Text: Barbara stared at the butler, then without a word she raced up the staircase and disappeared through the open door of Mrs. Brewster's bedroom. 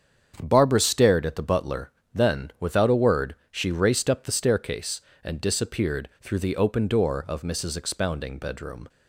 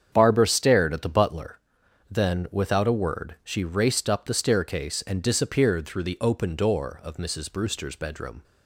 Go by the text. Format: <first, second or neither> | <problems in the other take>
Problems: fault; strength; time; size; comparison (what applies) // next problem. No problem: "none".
second | starts louder than the rest; strong; until 1.4 s; 8 dB; strong in the second // pauses between "word" and "she"; slight; at 3.3 s; 0.16 s long // says "Expounding" for "Brewster's"; at 7.7 s